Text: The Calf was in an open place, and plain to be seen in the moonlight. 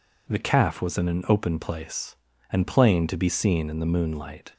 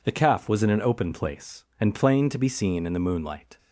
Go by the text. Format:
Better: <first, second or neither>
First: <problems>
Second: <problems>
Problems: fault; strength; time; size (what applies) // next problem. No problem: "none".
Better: neither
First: none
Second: none